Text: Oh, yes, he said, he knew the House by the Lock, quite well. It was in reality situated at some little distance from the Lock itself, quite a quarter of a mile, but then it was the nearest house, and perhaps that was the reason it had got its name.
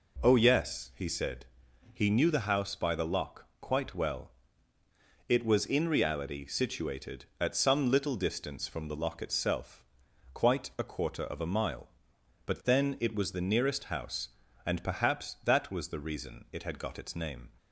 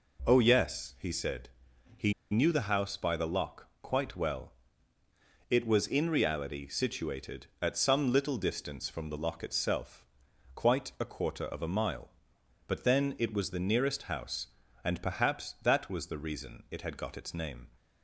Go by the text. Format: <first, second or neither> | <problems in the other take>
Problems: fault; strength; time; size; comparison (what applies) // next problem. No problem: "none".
first | pauses between "he" and "knew"; slight; at 2.1 s; 0.18 s long